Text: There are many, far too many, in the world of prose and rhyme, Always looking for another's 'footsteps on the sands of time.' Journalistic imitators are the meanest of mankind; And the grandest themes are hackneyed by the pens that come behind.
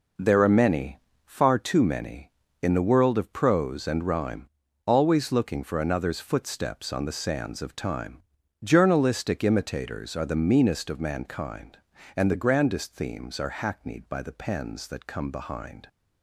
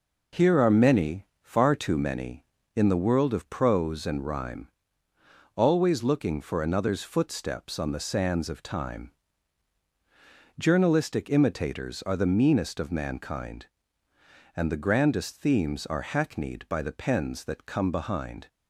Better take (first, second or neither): first